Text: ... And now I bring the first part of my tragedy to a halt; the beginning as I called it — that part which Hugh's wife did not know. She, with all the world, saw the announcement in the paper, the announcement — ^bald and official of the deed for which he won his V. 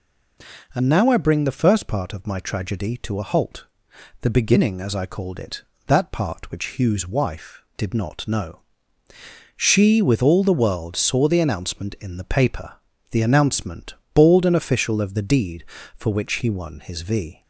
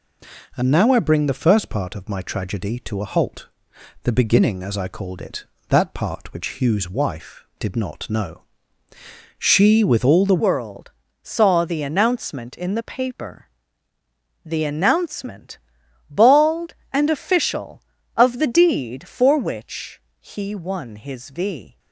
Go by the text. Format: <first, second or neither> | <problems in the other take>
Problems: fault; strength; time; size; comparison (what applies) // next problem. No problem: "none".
first | changes voice at "world"; from 10.3 s on; 11.4 s long // pauses between "which" and "he"; slight; at 19.9 s; 0.22 s long